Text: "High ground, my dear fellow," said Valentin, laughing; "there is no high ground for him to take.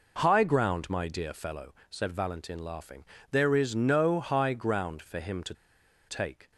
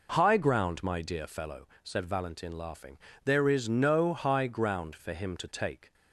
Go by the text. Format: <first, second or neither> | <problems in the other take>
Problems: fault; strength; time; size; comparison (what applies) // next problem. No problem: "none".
second | pauses between "to" and "take"; noticeable; at 5.5 s; 0.55 s long